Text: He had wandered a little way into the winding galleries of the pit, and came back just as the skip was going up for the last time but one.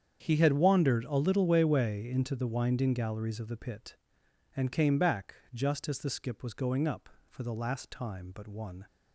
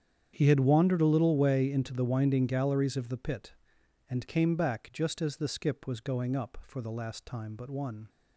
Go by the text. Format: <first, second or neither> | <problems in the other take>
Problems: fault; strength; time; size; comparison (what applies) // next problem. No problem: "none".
second | starts louder than the rest; strong; until 1.2 s; 8 dB; strong in the second // says "way" twice; at 1.6 s // pauses between "back" and "just"; slight; at 5.3 s; 0.18 s long